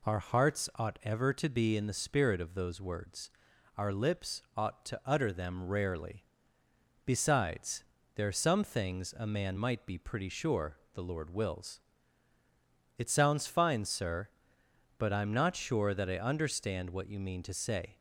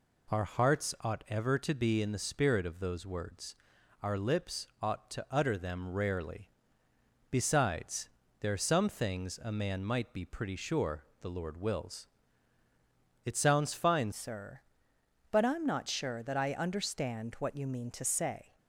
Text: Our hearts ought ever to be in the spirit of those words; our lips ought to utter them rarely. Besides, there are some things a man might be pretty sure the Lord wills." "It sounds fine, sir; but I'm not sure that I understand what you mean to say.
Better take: first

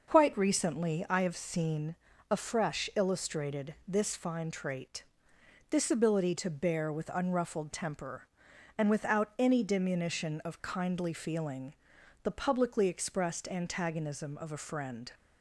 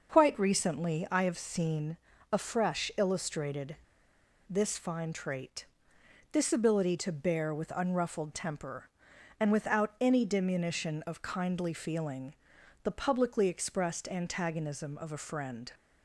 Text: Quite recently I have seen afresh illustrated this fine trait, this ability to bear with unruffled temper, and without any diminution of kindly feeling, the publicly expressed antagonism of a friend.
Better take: first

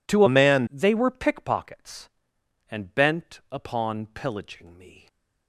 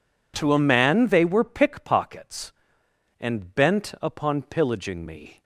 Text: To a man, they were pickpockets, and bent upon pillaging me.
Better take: second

